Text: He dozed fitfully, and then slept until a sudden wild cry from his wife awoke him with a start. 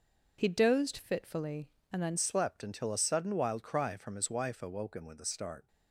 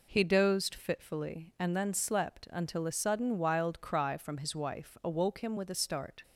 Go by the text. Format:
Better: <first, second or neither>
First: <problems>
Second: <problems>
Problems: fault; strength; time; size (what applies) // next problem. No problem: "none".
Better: second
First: changes voice at "slept"; from 2.1 s on; 3.5 s long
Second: none